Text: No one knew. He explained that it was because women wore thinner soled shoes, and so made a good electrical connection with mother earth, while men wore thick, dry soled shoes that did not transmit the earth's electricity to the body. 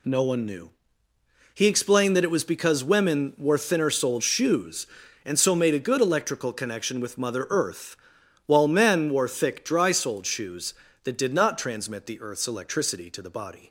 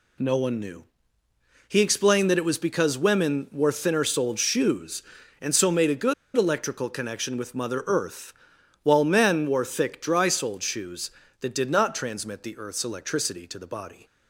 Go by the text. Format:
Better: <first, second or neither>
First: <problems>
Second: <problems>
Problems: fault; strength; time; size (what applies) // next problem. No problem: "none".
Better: first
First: none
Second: pauses between "good" and "electrical"; slight; at 6.1 s; 0.23 s long